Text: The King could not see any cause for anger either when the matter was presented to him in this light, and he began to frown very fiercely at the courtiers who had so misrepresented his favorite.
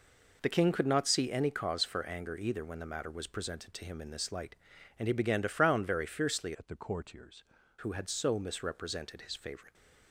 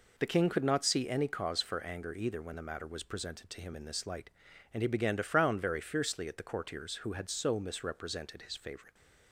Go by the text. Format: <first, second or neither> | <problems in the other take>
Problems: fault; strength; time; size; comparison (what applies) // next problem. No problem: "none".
second | changes voice from "at" to "courtiers"; from 6.5 to 7.4 s; 0.9 s long